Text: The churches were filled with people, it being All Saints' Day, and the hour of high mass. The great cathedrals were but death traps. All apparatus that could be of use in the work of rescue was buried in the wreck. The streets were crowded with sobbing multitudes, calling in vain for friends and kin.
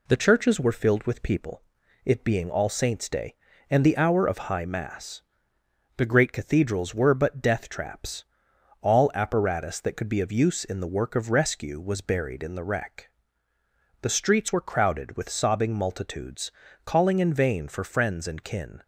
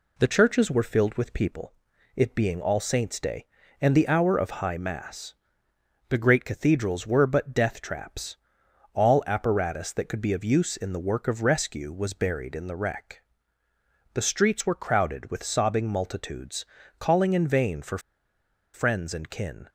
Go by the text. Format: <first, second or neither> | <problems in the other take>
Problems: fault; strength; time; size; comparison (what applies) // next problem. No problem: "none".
first | pauses between "for" and "friends"; noticeable; at 17.9 s; 0.75 s long